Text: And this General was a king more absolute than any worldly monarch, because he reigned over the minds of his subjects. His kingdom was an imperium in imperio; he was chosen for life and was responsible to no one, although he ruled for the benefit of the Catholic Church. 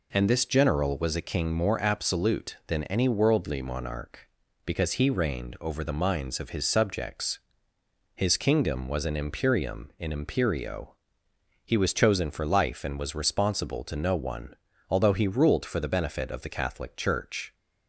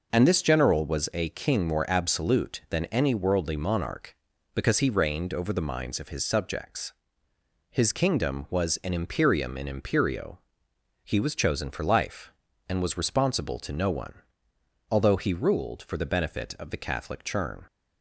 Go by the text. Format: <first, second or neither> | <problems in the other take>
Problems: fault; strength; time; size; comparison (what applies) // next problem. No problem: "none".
first | says "Churn" for "Church"; at 17.2 s